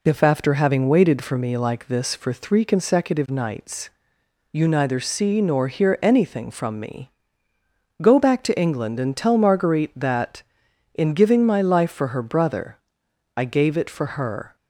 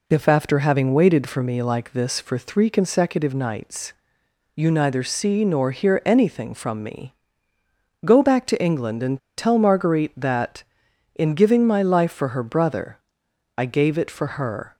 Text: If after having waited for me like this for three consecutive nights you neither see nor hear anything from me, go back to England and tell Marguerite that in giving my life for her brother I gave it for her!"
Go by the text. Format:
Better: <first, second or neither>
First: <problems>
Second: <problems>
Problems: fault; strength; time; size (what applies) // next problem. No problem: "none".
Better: first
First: pauses between "nights" and "you"; noticeable; at 3.8 s; 0.66 s long // pauses between "brother" and "I"; noticeable; at 12.7 s; 0.60 s long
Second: pauses between "nights" and "you"; noticeable; at 3.9 s; 0.66 s long // pauses between "and" and "tell"; slight; at 9.1 s; 0.18 s long // pauses between "brother" and "I"; noticeable; at 12.9 s; 0.60 s long